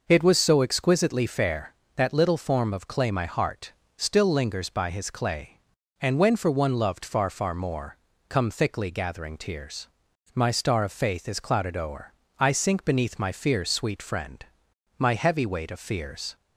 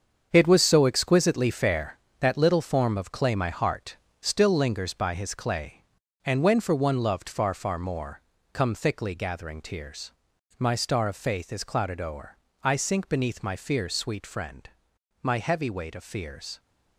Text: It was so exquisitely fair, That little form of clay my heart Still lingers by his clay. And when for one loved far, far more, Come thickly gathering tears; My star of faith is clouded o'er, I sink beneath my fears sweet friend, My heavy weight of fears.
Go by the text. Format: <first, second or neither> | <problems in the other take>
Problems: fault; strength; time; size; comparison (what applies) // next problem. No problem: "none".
first | gets quieter; strong; throughout; 8.5 dB // pauses between "heart" and "Still"; slight; at 3.9 s; 0.24 s long; slight in the first